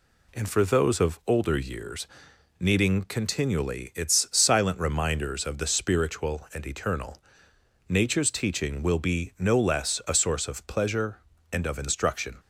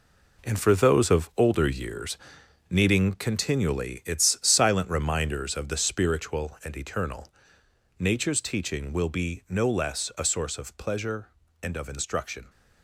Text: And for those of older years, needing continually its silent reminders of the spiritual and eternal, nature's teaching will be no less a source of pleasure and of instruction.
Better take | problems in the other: first | gets quieter; strong; throughout; 9 dB

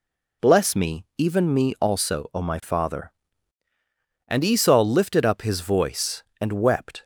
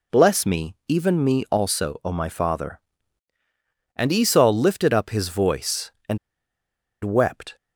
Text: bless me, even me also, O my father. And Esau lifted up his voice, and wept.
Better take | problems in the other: first | pauses between "and" and "wept"; noticeable; at 6.1 s; 0.85 s long

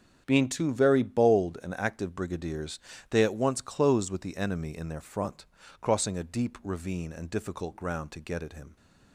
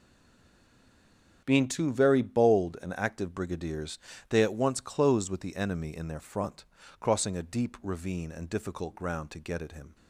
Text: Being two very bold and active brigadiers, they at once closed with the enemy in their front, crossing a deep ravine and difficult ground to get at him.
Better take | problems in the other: first | stays silent before the first word; noticeable; until 1.4 s; 1.4 s long // starts louder than the rest; strong; until 2.4 s; 7.5 dB; strong in the first

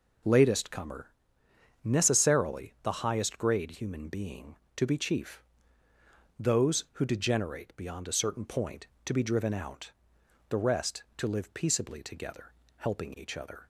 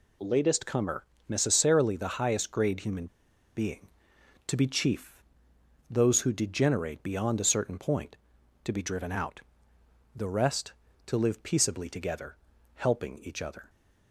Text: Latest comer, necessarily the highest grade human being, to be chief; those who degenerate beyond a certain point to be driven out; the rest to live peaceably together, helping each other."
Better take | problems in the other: first | pauses between "human" and "being"; noticeable; at 3.0 s; 0.50 s long

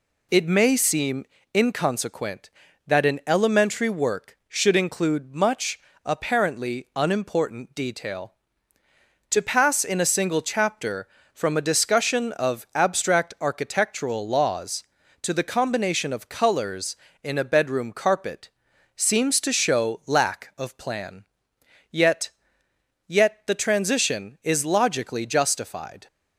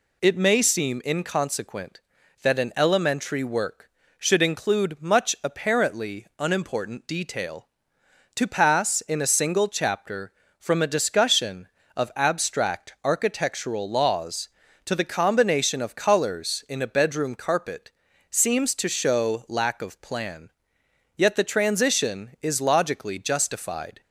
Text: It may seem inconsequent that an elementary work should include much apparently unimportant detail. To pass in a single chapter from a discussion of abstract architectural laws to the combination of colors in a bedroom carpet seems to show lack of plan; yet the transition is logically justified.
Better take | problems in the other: second | pauses between "seem" and "inconsequent"; slight; at 1.2 s; 0.30 s long // pauses between "much" and "apparently"; slight; at 5.7 s; 0.25 s long // pauses between "carpet" and "seems"; noticeable; at 18.4 s; 0.46 s long; also in the second // says "yet" twice; at 23.0 s

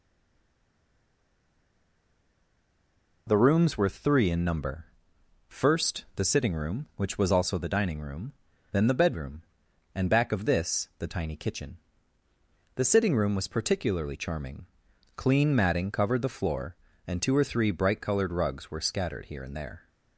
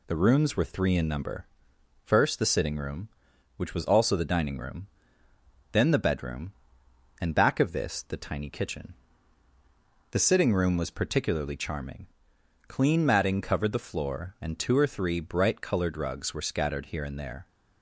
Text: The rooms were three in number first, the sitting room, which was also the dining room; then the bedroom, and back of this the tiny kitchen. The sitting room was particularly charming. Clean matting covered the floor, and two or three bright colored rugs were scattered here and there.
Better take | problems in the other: second | stays silent before the first word; strong; until 3.2 s; 3.2 s long // pauses between "number" and "first"; noticeable; at 4.8 s; 0.62 s long; noticeable in the second

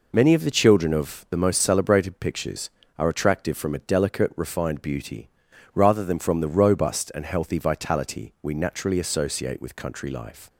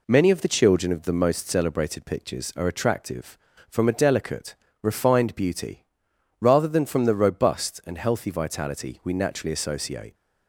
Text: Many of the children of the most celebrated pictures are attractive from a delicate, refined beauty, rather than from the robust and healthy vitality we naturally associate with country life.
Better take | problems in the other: first | stops before "with country life"; at 10.1 s

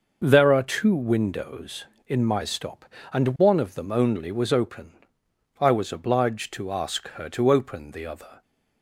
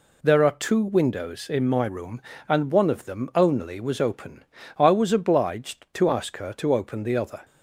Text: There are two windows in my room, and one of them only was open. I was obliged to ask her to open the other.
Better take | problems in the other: second | says "stop" for "room"; at 2.4 s

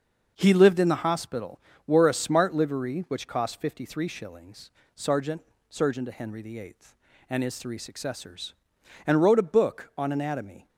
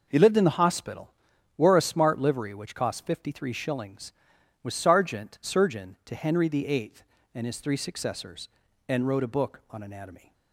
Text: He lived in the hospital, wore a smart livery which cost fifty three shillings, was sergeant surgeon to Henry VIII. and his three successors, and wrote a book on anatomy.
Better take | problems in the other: second | starts louder than the rest; until 1.3 s; 6 dB // skips "was"; at 4.8 s // pauses between "sergeant" and "surgeon"; slight; at 5.4 s; 0.28 s long

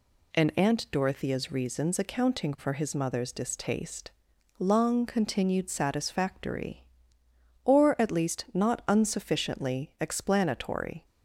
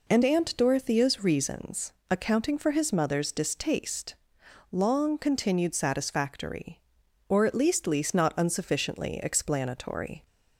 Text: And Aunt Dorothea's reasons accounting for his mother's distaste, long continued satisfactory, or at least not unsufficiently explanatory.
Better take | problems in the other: first | pauses between "reasons" and "accounting"; slight; at 1.9 s; 0.20 s long // says "least" twice; at 7.8 s

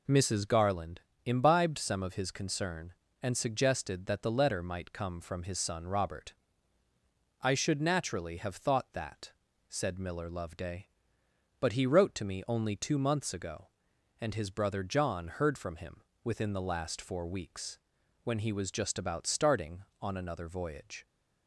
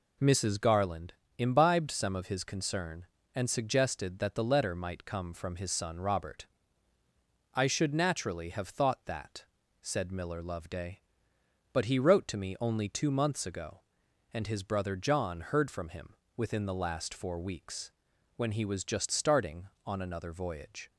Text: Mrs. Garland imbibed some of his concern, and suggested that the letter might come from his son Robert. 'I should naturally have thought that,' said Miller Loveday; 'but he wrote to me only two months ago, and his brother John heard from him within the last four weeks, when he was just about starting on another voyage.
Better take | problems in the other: first | pauses between "Garland" and "imbibed"; slight; at 1.1 s; 0.26 s long; slight in the first // pauses between "him" and "within"; slight; at 16.1 s; 0.20 s long; slight in the first // skips "about"; at 19.0 s

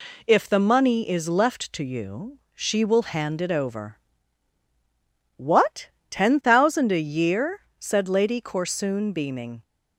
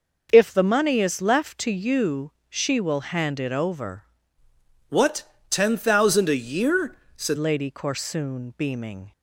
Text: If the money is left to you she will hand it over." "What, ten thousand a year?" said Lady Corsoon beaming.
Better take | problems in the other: first | pauses between "you" and "she"; slight; at 2.3 s; 0.18 s long; slight in the first // changes voice from "What" to "said"; from 4.8 to 7.3 s; 2.5 s long

